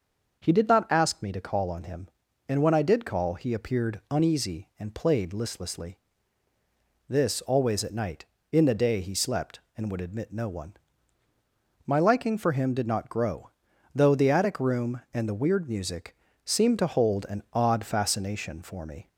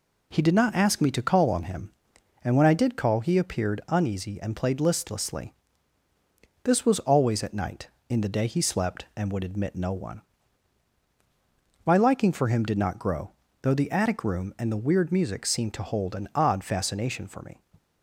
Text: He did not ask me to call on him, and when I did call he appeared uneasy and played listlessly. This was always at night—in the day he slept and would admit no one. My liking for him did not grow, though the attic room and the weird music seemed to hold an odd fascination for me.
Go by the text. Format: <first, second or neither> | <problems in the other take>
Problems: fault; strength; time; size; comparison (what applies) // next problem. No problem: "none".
second | starts louder than the rest; until 1.4 s; 6.5 dB // skips "was"; at 7.4 s // pauses between "music" and "seemed"; slight; at 16.1 s; 0.28 s long